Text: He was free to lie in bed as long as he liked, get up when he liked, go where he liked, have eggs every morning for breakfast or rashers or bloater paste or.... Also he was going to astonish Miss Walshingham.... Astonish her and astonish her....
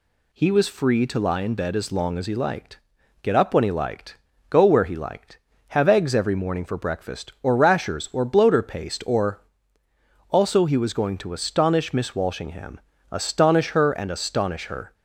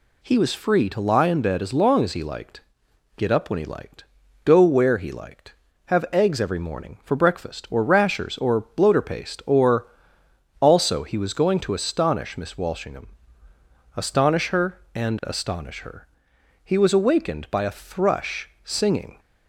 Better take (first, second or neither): first